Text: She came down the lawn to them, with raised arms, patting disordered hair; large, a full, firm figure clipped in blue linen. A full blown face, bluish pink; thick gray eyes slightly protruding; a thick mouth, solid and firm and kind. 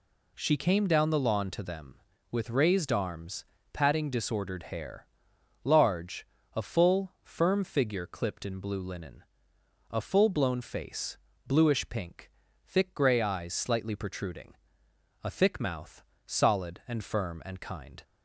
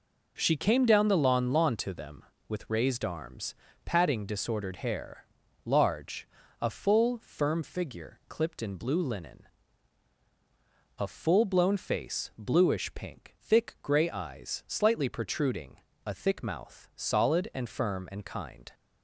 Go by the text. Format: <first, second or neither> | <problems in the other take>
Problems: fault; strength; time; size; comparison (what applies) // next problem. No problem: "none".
first | says "lawn" twice; at 1.5 s